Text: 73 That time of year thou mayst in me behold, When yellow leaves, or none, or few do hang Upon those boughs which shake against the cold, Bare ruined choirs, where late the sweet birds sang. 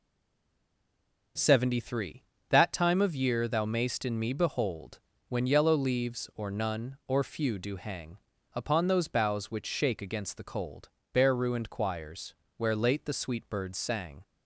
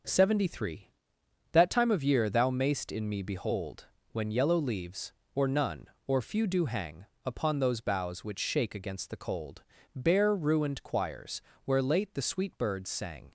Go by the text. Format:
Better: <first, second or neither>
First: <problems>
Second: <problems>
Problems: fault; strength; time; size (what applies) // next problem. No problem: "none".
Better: second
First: stays silent before the first word; noticeable; until 1.3 s; 1.3 s long // starts louder than the rest; noticeable; until 2.6 s; 6 dB // pauses between "hang" and "Upon"; at 8.1 s; 0.38 s long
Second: starts louder than the rest; until 1.7 s; 6.5 dB // pauses between "hang" and "Upon"; slight; at 7.0 s; 0.20 s long